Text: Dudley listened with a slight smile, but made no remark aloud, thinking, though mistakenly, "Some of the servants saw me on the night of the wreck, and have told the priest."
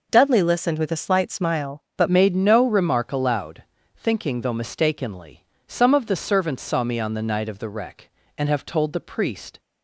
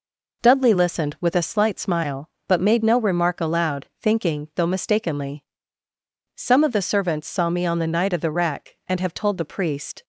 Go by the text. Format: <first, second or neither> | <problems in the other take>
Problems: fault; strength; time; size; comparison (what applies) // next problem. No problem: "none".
second | changes voice at "made"; from 2.0 s on; 7.5 s long